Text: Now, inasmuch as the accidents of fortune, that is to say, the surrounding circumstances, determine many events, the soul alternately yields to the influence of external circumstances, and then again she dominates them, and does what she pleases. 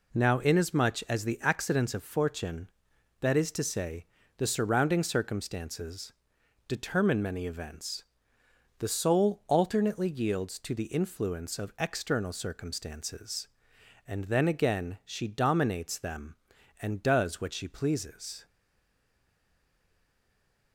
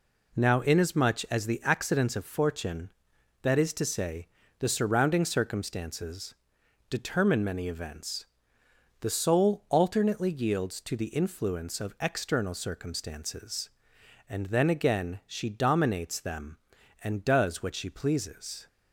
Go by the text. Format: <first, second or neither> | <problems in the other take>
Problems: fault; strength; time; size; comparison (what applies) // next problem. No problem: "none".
second | stays silent after the last word; from 18.4 s on; 2.3 s long